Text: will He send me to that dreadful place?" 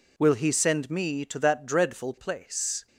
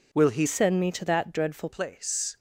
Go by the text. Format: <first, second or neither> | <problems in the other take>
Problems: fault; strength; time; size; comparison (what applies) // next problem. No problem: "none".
first | changes voice from "send" to "dreadful"; from 0.4 to 1.6 s; 1.2 s long